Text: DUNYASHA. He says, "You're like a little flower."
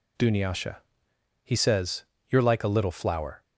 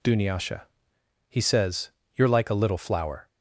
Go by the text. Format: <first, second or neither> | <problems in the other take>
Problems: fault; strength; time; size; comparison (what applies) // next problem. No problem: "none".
neither | none